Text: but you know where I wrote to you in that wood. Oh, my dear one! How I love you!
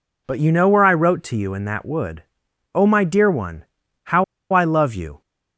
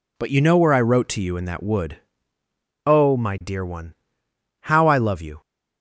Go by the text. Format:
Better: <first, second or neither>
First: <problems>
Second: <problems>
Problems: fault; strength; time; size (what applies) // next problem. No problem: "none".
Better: second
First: pauses between "How" and "I"; slight; at 4.2 s; 0.28 s long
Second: none